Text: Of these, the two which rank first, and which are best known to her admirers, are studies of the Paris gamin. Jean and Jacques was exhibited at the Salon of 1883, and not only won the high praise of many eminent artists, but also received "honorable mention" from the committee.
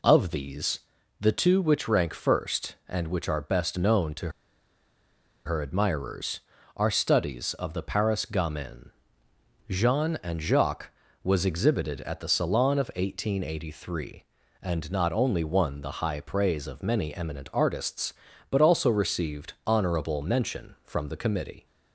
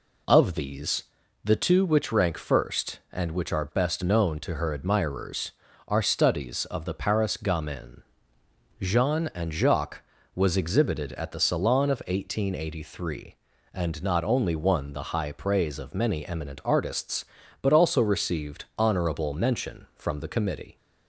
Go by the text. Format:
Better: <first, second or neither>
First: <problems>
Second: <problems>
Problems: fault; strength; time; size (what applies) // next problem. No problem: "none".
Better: second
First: pauses between "to" and "her"; at 4.2 s; 1.1 s long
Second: none